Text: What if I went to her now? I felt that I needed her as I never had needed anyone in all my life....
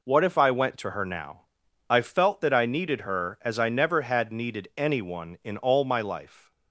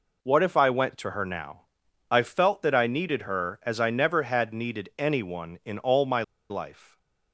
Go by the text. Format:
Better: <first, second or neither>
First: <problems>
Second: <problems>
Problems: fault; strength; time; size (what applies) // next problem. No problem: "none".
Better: first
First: none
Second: pauses between "my" and "life"; slight; at 6.2 s; 0.27 s long